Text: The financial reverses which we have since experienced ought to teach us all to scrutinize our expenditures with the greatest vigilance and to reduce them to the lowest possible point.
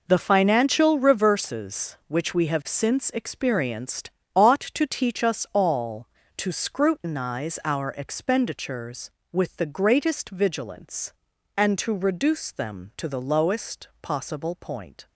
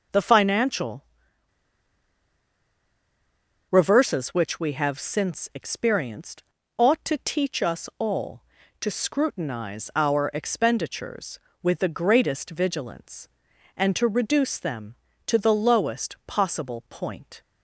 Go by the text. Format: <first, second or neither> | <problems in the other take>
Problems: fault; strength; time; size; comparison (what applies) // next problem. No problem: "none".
first | pauses between "financial" and "reverses"; strong; at 1.0 s; 2.6 s long // pauses between "experienced" and "ought"; slight; at 6.4 s; 0.34 s long; slight in the first